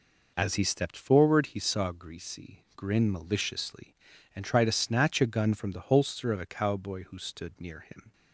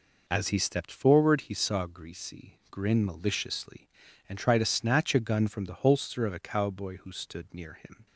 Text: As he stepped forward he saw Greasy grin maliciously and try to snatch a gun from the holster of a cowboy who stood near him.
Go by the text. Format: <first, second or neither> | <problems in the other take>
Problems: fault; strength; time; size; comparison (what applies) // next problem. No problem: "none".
neither | none